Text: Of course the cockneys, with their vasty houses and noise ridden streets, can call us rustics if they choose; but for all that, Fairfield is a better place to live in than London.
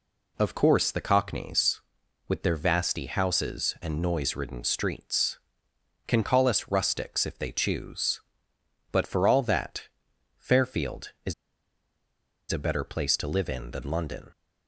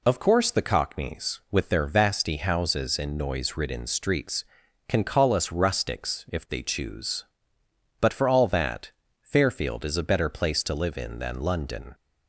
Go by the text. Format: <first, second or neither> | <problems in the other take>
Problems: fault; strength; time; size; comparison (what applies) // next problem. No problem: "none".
second | pauses between "is" and "a"; at 11.3 s; 1.1 s long